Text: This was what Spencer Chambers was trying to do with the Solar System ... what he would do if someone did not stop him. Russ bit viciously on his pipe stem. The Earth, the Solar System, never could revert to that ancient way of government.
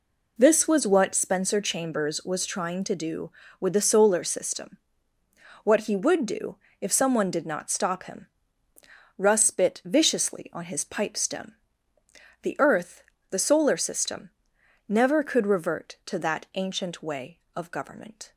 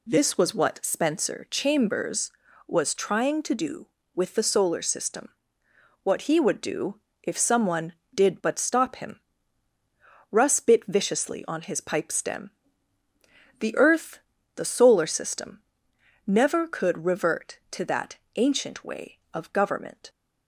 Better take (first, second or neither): first